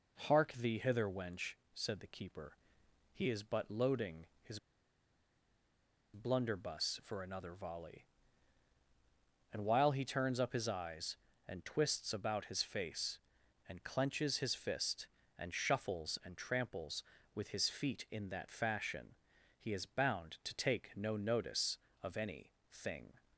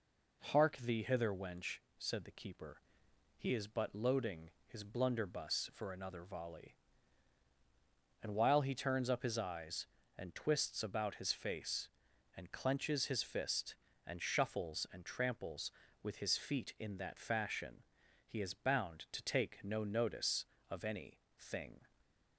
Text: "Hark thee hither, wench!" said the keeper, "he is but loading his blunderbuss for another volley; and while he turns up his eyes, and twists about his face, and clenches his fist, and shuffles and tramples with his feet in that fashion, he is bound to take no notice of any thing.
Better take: second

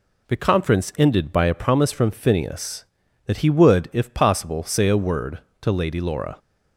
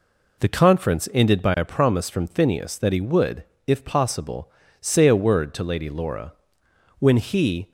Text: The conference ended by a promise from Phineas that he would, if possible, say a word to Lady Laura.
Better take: first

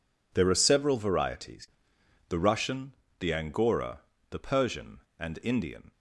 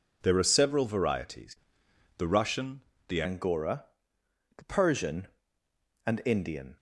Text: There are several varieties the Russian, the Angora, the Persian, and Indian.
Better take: first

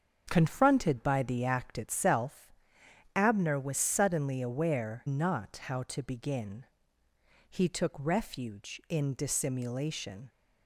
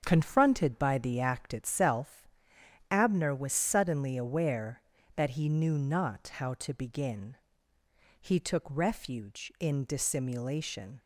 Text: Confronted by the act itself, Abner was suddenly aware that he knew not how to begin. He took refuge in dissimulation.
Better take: second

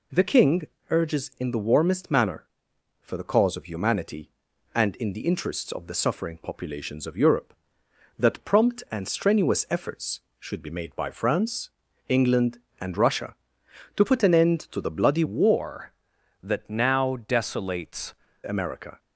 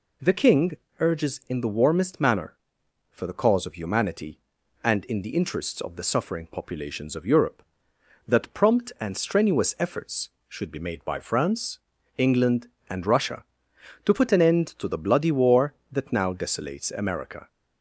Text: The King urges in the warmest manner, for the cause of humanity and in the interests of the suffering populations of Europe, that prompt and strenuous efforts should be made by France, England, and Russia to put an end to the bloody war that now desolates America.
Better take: second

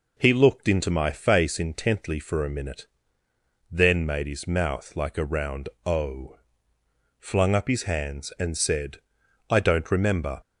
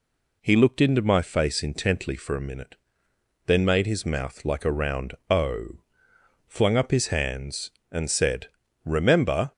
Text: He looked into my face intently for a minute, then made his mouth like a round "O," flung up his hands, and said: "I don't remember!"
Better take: first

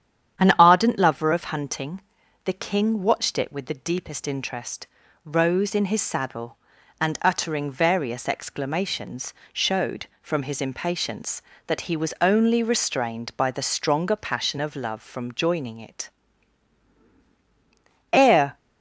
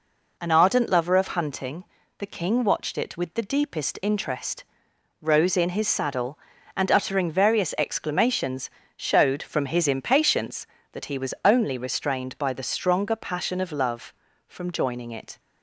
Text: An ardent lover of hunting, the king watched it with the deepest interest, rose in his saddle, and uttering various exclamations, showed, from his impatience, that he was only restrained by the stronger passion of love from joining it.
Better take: second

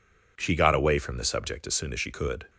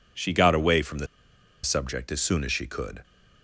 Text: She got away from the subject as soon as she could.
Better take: first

